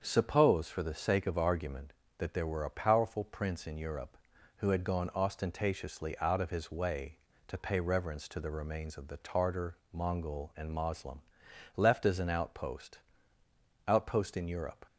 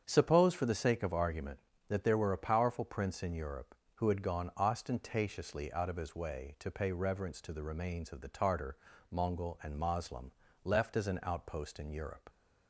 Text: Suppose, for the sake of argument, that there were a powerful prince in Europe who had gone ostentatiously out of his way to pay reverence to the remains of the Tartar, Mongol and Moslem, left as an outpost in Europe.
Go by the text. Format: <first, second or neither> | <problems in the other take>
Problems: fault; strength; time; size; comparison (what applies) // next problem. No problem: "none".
second | starts louder than the rest; until 1.0 s; 7 dB; strong in the second // says "outpost" twice; at 13.8 s